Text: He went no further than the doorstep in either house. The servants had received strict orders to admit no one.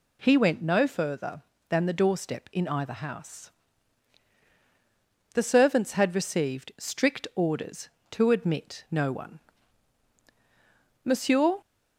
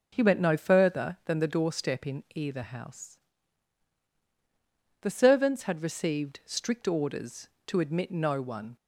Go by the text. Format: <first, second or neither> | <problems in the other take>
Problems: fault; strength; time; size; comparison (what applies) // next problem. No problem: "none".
second | goes on to say "Monsieur"; from 11.0 s on; 0.52 s long